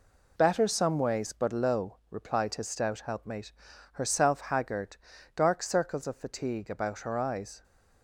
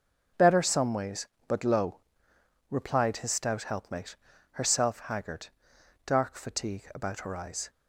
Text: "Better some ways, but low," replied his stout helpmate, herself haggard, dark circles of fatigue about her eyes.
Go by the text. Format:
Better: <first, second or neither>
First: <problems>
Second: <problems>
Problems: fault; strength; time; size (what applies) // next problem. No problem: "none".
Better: first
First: none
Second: skips "circles of"; at 6.3 s